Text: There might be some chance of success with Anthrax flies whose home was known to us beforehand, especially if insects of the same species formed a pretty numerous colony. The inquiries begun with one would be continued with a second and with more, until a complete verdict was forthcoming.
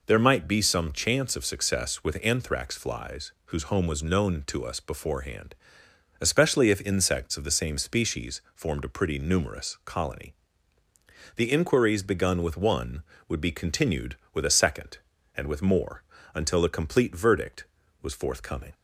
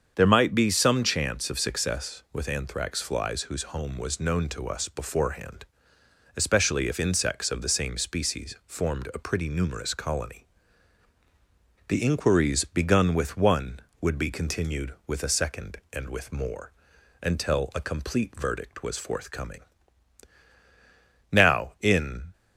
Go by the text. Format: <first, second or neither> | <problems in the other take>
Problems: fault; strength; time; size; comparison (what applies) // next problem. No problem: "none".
first | starts louder than the rest; strong; until 1.1 s; 7.5 dB // goes on to say "Now in"; noticeable; from 21.3 s on; 1.0 s long